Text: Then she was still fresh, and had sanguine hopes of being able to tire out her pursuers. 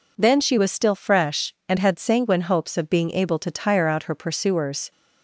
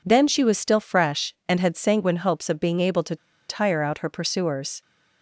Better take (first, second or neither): first